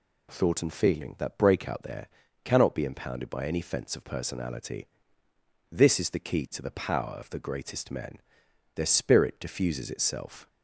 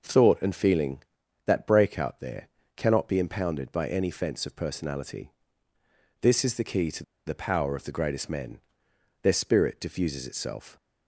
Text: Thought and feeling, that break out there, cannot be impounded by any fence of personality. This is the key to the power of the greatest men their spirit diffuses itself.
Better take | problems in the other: first | pauses between "to" and "the"; slight; at 7.0 s; 0.23 s long // pauses between "men" and "their"; noticeable; at 8.5 s; 0.64 s long; noticeable in the first

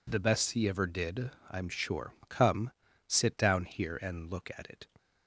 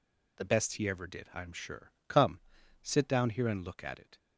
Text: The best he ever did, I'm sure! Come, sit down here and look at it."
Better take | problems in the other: neither | none

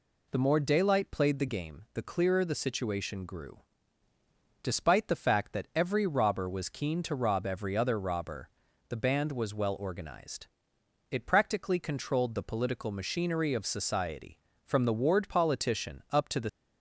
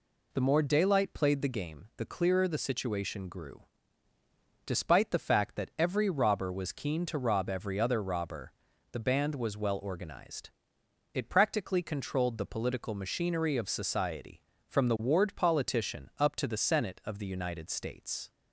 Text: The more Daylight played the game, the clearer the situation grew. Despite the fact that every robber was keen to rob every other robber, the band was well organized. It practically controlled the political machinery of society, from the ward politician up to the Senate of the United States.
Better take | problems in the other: second | stops before "Senate of the United States"; at 16.4 s

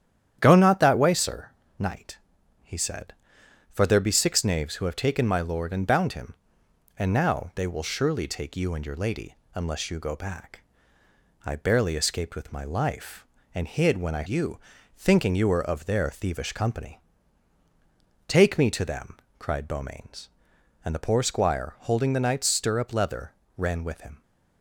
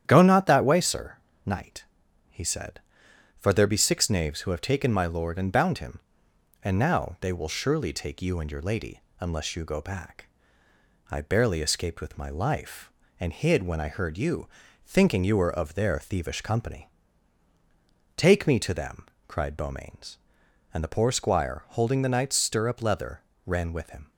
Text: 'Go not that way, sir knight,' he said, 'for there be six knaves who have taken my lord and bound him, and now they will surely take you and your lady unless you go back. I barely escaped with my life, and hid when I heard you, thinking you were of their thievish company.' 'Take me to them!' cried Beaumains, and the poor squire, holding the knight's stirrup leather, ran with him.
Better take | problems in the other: second | starts louder than the rest; strong; until 1.4 s; 10 dB; strong in the second // pauses between "sir" and "knight"; slight; at 1.4 s; 0.28 s long; slight in the second // pauses between "lady" and "unless"; slight; at 9.3 s; 0.18 s long; slight in the second // skips "heard"; at 14.2 s

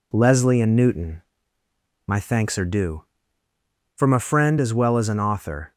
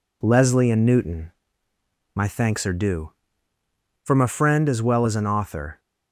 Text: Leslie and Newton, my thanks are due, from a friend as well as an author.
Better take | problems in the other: neither | none

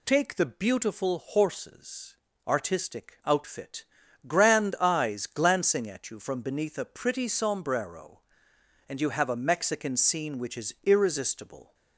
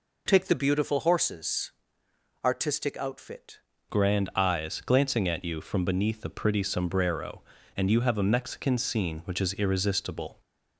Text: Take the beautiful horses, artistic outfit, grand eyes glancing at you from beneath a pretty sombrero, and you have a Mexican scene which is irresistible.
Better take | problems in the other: first | changes voice at "grand"; from 3.8 s on; 6.5 s long

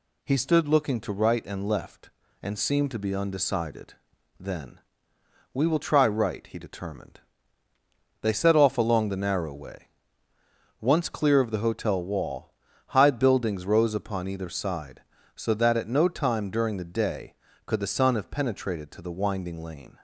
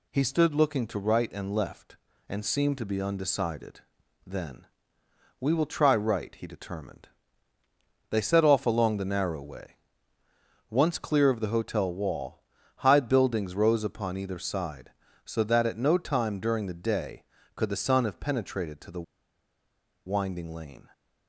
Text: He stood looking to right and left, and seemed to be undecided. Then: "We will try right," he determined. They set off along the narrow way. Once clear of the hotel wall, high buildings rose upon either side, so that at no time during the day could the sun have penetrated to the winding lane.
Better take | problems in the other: first | pauses between "the" and "winding"; at 19.0 s; 1.0 s long

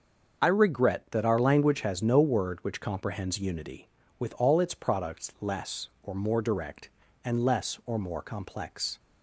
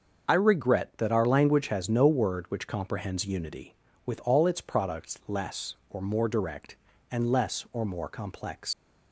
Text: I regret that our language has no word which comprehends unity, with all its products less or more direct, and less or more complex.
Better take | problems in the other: first | starts louder than the rest; until 1.2 s; 6.5 dB; also in the first // leaves "complex" unfinished; at 8.7 s; 125 ms

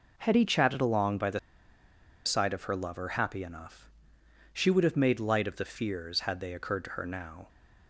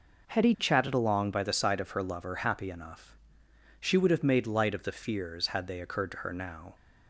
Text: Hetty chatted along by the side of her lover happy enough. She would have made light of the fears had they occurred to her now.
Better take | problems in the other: second | pauses between "the" and "side"; noticeable; at 1.3 s; 0.86 s long

